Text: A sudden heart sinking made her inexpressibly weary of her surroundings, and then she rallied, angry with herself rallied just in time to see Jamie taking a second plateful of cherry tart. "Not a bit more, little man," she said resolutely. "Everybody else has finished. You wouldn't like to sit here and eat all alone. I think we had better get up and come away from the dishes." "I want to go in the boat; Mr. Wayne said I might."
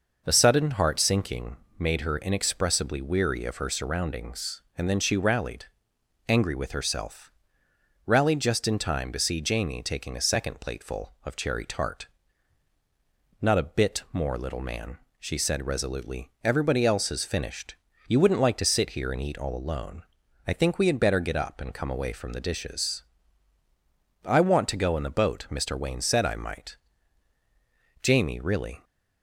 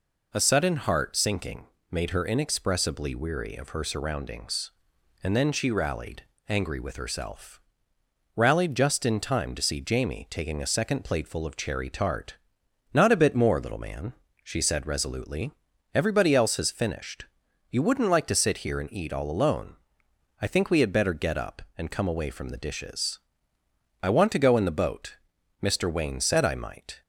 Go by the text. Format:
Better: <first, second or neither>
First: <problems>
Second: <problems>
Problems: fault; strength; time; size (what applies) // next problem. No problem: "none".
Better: second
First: pauses between "sinking" and "made"; slight; at 1.5 s; 0.20 s long // pauses between "herself" and "rallied"; noticeable; at 7.2 s; 0.76 s long // goes on to say "Jamie really"; noticeable; from 28.0 s on; 0.82 s long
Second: pauses between "sinking" and "made"; slight; at 1.6 s; 0.22 s long // pauses between "herself" and "rallied"; noticeable; at 7.5 s; 0.76 s long